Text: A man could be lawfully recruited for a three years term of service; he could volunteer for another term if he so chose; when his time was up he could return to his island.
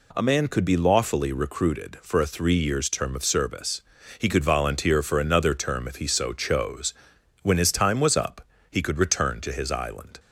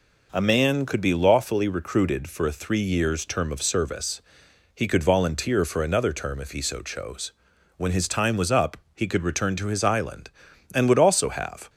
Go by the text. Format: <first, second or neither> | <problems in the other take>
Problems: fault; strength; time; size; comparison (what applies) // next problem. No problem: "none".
first | pauses between "up" and "he"; slight; at 8.7 s; 0.16 s long; slight in the first // goes on to say "And would also have"; noticeable; from 10.7 s on; 0.98 s long